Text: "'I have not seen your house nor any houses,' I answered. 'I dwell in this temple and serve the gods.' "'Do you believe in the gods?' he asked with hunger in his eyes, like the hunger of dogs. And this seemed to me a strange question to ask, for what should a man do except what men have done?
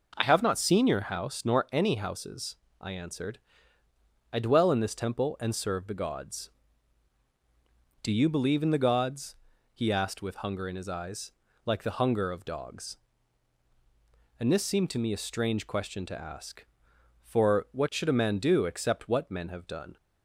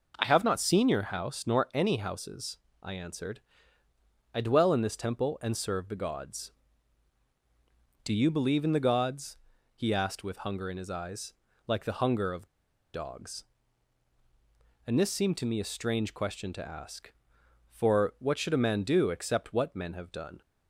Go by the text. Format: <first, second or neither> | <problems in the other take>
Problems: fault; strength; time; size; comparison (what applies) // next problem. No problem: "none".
first | pauses between "of" and "dogs"; noticeable; at 12.4 s; 0.48 s long